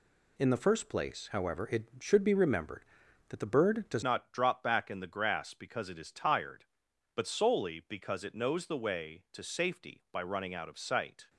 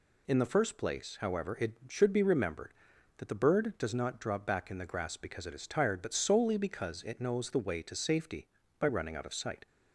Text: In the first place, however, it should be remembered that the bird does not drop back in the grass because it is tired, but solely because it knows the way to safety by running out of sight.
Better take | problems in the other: second | changes voice at "not"; from 4.0 s on; 7.2 s long

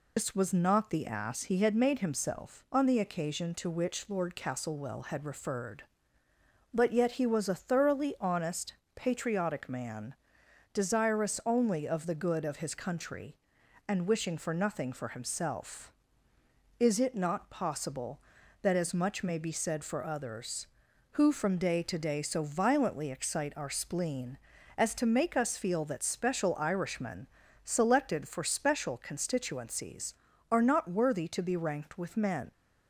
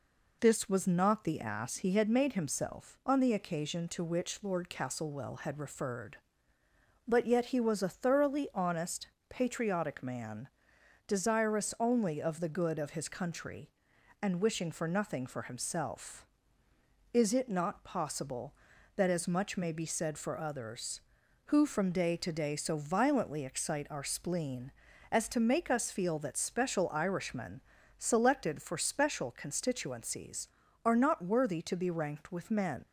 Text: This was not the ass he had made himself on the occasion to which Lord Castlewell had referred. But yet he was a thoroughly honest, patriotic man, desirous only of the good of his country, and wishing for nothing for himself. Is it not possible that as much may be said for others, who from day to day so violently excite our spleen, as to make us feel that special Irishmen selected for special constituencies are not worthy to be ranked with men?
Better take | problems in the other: second | loses the start of "This"; at 0.1 s; 90 ms // pauses between "Irishmen" and "selected"; slight; at 27.2 s; 0.36 s long; slight in the second

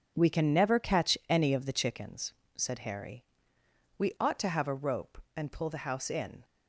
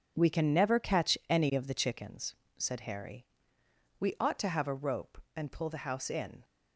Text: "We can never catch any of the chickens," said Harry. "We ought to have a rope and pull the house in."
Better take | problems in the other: neither | none

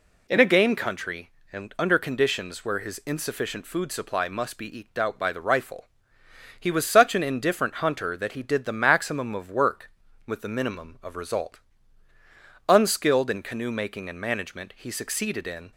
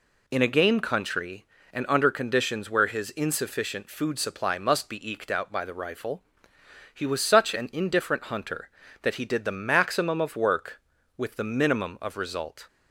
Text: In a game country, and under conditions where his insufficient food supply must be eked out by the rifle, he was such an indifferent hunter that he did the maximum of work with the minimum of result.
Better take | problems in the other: second | goes on to say "Unskilled in canoe making and management he succeeded in"; strong; from 12.6 s on; 3.0 s long

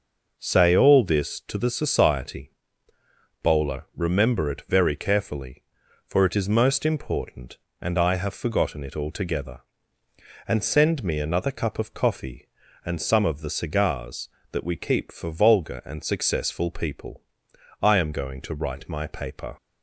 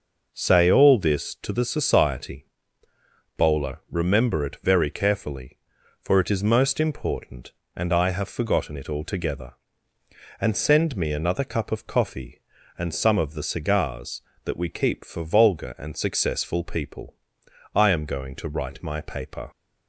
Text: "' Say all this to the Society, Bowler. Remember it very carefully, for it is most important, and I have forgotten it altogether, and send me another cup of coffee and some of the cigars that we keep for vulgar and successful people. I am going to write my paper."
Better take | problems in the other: neither | none

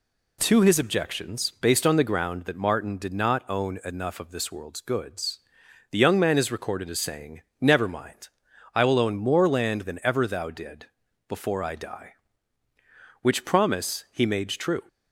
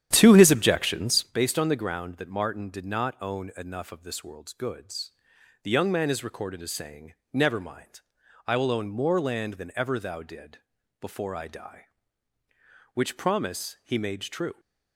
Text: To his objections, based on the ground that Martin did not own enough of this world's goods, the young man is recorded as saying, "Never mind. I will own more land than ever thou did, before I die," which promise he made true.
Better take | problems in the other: first | starts louder than the rest; strong; until 1.3 s; 10 dB

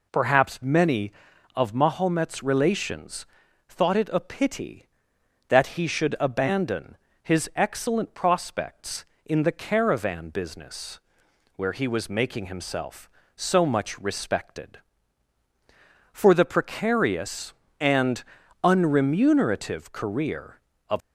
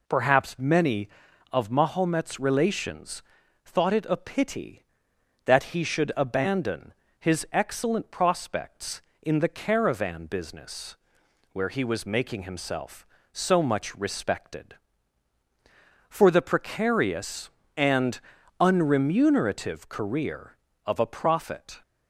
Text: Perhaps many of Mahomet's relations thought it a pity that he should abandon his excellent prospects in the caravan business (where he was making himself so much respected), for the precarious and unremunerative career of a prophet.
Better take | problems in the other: second | pauses between "relations" and "thought"; at 3.2 s; 0.42 s long; also in the second // pauses between "abandon" and "his"; slight; at 6.9 s; 0.26 s long; slight in the second // pauses between "and" and "unremunerative"; at 18.2 s; 0.40 s long; also in the second // stops before "a prophet"; at 21.0 s

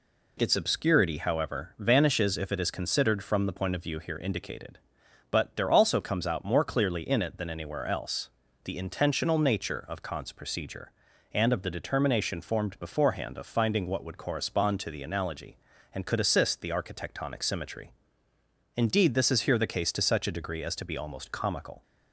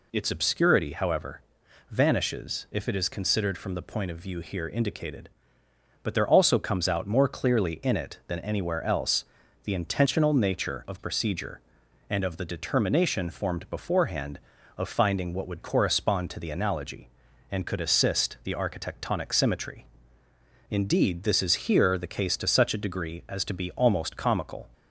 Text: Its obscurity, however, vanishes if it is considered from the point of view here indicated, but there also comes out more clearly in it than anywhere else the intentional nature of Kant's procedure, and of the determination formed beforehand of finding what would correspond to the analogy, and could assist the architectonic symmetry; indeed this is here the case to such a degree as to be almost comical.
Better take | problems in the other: first | pauses between "else" and "the"; at 9.2 s; 0.40 s long; slight in the first // skips "Kant's"; at 10.9 s

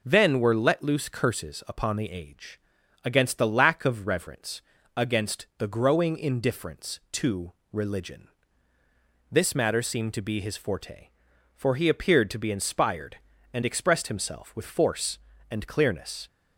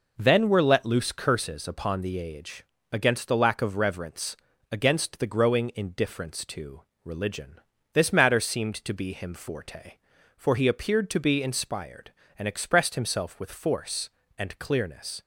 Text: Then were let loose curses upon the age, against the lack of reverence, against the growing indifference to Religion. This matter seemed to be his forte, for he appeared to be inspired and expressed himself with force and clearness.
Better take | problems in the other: first | pauses between "to" and "Religion"; slight; at 6.8 s; 0.22 s long; slight in the first // says "him" for "his"; at 9.1 s

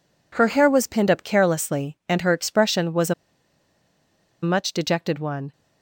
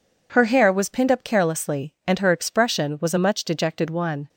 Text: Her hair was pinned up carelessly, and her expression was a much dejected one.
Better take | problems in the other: second | pauses between "a" and "much"; strong; at 3.1 s; 1.2 s long

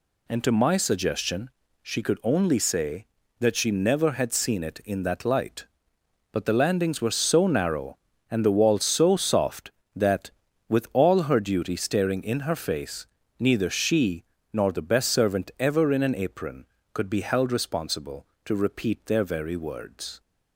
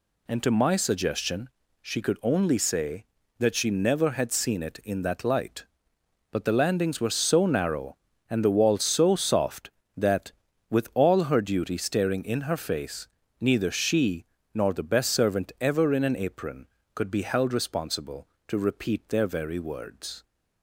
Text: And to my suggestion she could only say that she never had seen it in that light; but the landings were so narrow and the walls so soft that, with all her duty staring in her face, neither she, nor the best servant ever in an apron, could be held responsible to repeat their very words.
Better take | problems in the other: neither | pauses between "suggestion" and "she"; slight; the same in both

